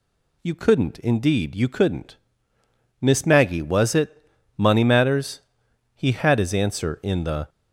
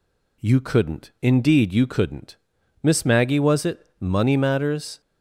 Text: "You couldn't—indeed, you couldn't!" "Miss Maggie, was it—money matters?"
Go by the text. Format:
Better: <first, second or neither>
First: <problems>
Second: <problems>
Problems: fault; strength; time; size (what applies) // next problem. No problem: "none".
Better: second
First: goes on to say "He had his answer in the"; from 5.9 s on; 1.5 s long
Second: none